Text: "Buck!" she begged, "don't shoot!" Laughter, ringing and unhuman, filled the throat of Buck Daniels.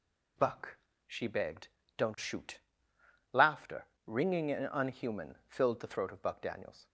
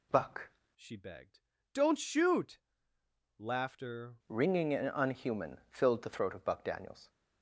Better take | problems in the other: first | changes voice from "she" to "Laughter"; from 0.7 to 4.1 s; 3.4 s long

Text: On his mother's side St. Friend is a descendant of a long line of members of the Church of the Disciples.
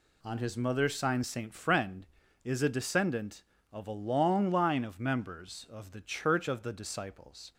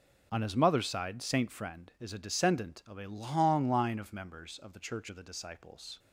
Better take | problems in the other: second | says "sign" for "side"; at 0.9 s

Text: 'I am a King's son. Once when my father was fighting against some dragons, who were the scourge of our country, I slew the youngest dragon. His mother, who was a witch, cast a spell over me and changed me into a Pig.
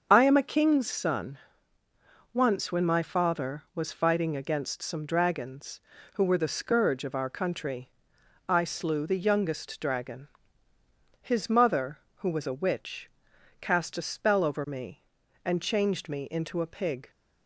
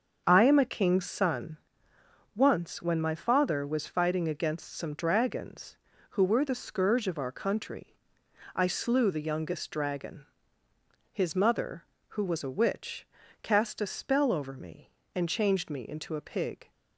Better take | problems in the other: neither | starts louder than the rest; the same in both

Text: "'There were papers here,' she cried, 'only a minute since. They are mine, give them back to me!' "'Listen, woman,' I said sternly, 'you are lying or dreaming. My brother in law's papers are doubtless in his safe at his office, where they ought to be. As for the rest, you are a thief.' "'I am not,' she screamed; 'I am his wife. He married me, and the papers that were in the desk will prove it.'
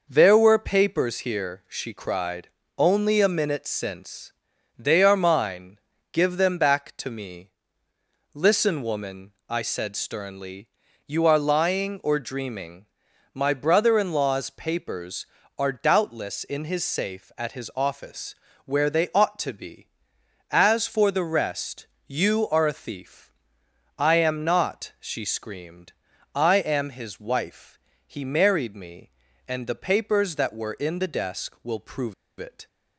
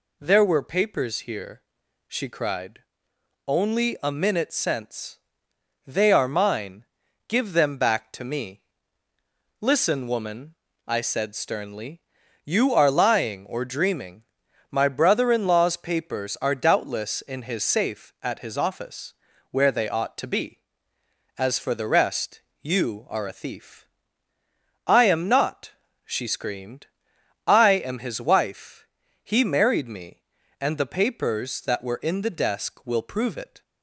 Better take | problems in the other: second | pauses between "prove" and "it"; slight; at 32.1 s; 0.26 s long

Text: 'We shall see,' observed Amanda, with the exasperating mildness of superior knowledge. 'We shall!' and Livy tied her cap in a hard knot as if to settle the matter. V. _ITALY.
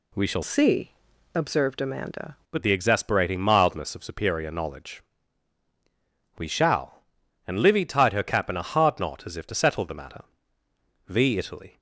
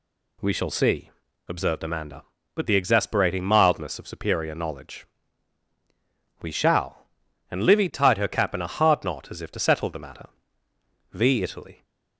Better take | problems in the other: second | changes voice from "see" to "Amanda"; from 0.4 to 2.3 s; 1.9 s long

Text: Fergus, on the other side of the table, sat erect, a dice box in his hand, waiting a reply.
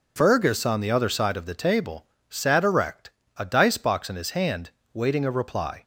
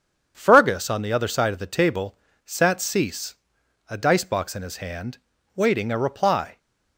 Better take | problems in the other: first | starts louder than the rest; strong; until 1.3 s; 7.5 dB // says "cease" for "erect"; at 2.8 s

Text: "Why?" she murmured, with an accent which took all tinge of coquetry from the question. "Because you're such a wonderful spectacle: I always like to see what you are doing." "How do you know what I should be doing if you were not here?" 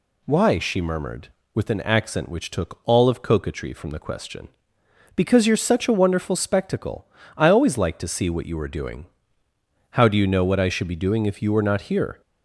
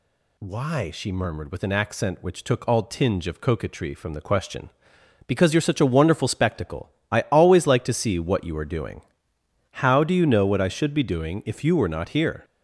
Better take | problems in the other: second | skips "tinge"; at 3.0 s

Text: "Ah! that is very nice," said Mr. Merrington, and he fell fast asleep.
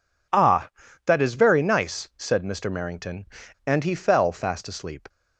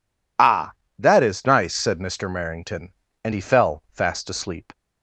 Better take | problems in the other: first | skips "very"; at 1.4 s

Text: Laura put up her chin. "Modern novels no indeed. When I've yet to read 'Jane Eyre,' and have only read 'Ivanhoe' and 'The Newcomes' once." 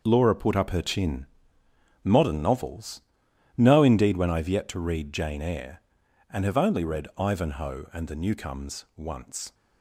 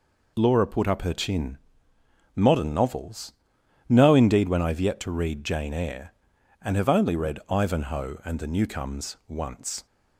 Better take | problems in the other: second | gets quieter; strong; throughout; 9.5 dB // pauses between "novels" and "no"; noticeable; at 3.0 s; 0.54 s long; noticeable in the second

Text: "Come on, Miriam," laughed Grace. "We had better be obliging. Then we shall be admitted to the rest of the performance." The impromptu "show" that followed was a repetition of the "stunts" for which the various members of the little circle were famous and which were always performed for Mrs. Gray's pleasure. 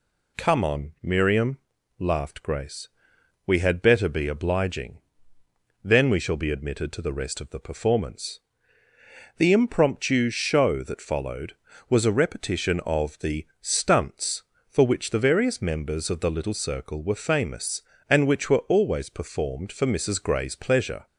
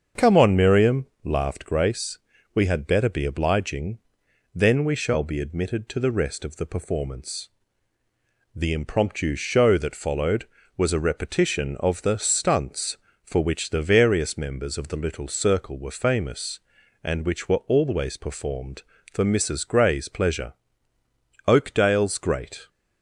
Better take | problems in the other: first | starts louder than the rest; until 1.3 s; 7 dB // goes on to say "Oakdale's Great"; noticeable; from 21.4 s on; 1.2 s long

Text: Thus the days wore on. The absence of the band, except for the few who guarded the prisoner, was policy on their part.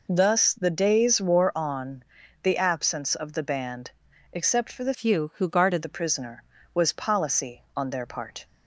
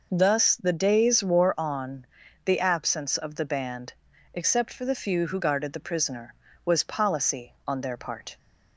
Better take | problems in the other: second | changes voice from "few" to "guarded"; from 4.9 to 5.8 s; 0.9 s long

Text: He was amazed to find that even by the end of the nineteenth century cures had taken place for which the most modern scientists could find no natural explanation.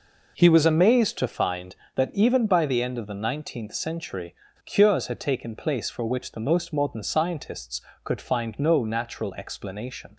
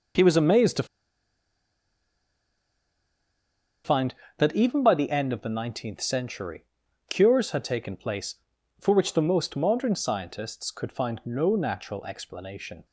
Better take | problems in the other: first | pauses between "to" and "find"; strong; at 0.8 s; 2.9 s long // pauses between "century" and "cures"; noticeable; at 6.6 s; 0.46 s long; slight in the first

